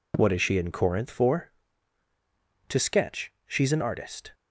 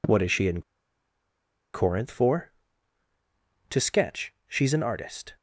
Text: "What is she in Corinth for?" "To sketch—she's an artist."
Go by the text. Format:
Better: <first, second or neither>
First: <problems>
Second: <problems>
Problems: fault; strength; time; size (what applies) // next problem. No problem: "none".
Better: first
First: none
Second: pauses between "in" and "Corinth"; at 0.6 s; 1.1 s long